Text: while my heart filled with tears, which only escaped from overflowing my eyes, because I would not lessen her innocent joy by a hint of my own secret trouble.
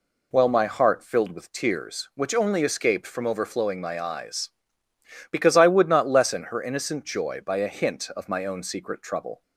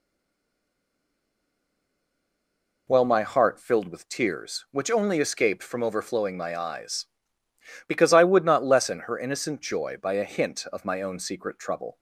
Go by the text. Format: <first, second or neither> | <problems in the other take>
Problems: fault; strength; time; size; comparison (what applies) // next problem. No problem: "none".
first | stays silent before the first word; strong; until 2.8 s; 2.8 s long